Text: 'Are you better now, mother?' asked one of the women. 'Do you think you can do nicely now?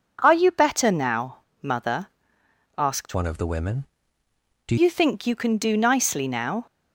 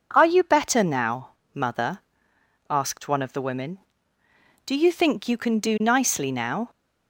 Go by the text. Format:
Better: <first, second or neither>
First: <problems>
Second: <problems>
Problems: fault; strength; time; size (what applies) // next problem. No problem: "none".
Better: second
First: changes voice from "one" to "Do"; from 3.1 to 4.7 s; 1.6 s long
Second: none